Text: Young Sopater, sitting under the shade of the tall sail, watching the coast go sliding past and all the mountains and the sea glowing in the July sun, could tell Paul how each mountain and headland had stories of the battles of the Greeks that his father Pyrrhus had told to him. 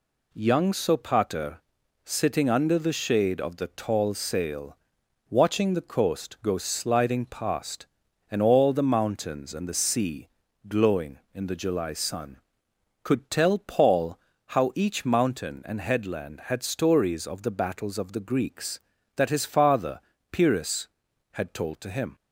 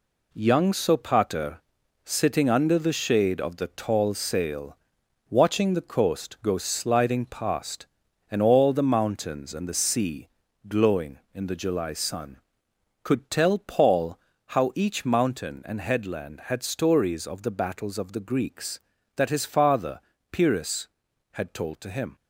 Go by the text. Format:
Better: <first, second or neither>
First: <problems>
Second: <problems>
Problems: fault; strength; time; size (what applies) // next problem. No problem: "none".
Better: first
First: pauses between "sea" and "glowing"; at 10.2 s; 0.40 s long // pauses between "Paul" and "how"; slight; at 14.1 s; 0.30 s long // pauses between "father" and "Pyrrhus"; slight; at 19.9 s; 0.32 s long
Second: gets quieter; throughout; 6.5 dB // pauses between "sea" and "glowing"; at 10.2 s; 0.40 s long // pauses between "Paul" and "how"; slight; at 14.1 s; 0.30 s long // pauses between "father" and "Pyrrhus"; slight; at 19.9 s; 0.32 s long